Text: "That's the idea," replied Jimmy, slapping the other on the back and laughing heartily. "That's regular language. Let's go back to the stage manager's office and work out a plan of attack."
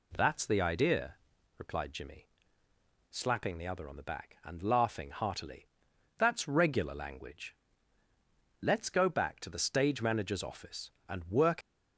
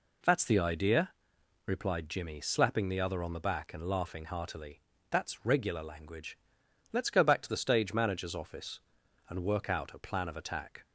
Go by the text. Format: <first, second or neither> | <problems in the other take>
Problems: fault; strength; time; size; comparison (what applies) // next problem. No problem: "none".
second | stops before "out a plan of attack"; at 11.6 s